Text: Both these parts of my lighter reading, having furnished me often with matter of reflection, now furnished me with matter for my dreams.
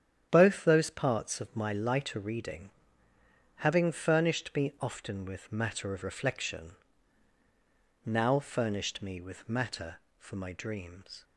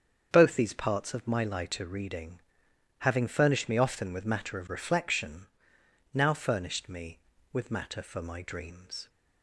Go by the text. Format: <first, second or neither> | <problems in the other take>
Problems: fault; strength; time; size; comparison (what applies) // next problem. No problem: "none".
second | starts louder than the rest; strong; until 1.3 s; 9 dB; strong in the second // says "those" for "these"; at 0.6 s